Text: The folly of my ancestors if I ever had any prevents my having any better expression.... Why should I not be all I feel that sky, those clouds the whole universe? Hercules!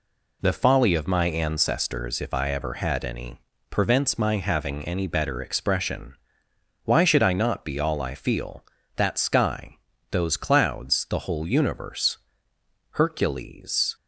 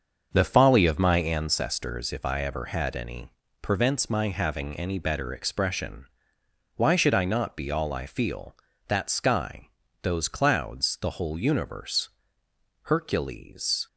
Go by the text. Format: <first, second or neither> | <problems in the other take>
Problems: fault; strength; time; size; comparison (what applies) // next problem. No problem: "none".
first | starts louder than the rest; until 1.4 s; 6.5 dB // pauses between "any" and "prevents"; slight; at 3.3 s; 0.30 s long; slight in the first